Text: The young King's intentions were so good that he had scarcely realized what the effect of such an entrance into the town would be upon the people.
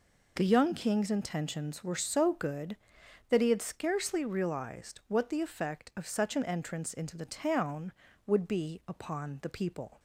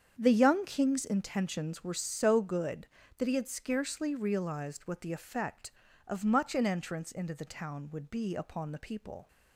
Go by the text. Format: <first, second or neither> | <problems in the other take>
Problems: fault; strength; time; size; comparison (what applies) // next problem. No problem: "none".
first | starts louder than the rest; strong; until 1.2 s; 7.5 dB // says "much" for "such"; at 6.2 s